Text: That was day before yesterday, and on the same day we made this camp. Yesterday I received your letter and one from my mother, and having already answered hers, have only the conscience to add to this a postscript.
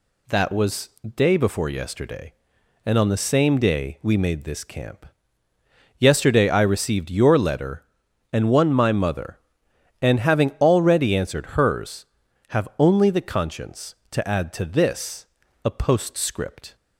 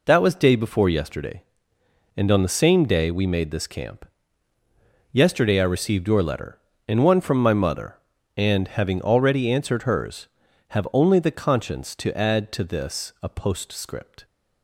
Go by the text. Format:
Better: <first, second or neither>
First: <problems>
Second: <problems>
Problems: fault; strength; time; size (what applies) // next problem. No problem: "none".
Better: second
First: pauses between "was" and "day"; slight; at 0.8 s; 0.26 s long // skips "from"; at 8.7 s // pauses between "this" and "a"; at 15.2 s; 0.40 s long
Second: none